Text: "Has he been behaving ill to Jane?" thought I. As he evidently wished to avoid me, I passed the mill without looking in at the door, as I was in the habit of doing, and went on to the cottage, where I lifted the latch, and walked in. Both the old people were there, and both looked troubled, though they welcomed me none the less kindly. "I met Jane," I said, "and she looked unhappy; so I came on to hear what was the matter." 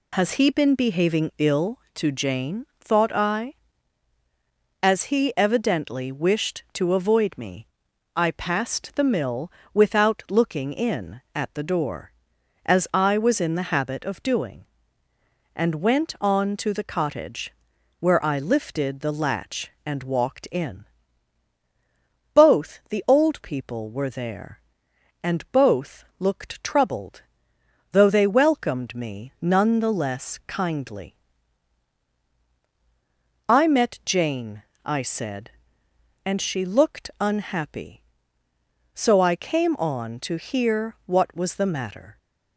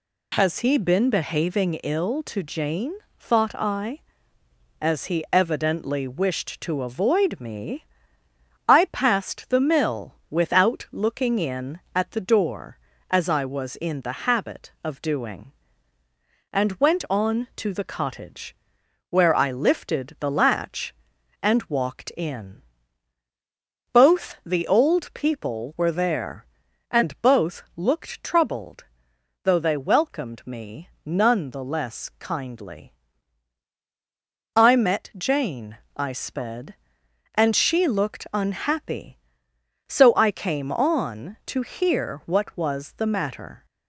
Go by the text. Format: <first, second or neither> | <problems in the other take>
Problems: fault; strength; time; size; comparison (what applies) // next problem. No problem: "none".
first | pauses between "mill" and "without"; slight; at 10.1 s; 0.16 s long; slight in the first // pauses between "both" and "looked"; slight; at 27.6 s; 0.16 s long; slight in the first // pauses between "me" and "none"; slight; at 30.8 s; 0.18 s long // says "sped" for "said"; at 36.1 s